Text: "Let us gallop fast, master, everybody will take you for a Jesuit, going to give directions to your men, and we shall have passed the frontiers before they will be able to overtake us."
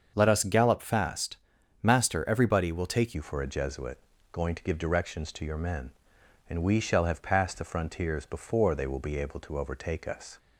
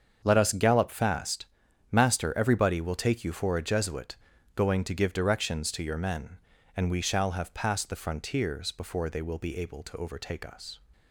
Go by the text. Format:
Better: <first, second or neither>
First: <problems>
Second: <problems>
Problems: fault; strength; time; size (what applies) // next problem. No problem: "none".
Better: second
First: starts louder than the rest; until 1.1 s; 6.5 dB // changes voice at "you"; from 3.1 s on; 7.2 s long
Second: starts louder than the rest; until 1.2 s; 7 dB